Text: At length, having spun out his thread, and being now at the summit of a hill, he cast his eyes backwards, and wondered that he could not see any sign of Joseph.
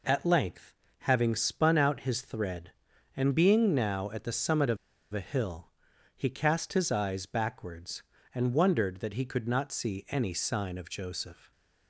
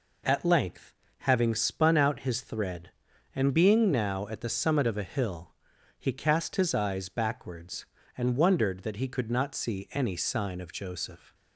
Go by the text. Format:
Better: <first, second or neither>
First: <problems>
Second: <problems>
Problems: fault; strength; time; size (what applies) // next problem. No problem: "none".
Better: second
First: pauses between "of" and "a"; slight; at 4.7 s; 0.36 s long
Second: none